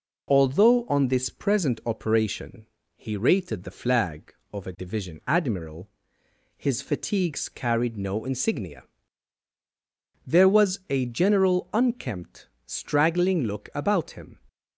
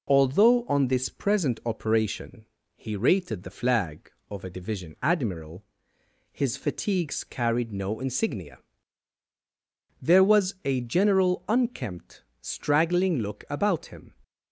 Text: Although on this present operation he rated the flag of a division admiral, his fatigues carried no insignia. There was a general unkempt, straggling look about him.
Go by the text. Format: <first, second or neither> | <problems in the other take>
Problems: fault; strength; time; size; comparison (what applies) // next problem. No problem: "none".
neither | pauses between "operation" and "he"; slight; the same in both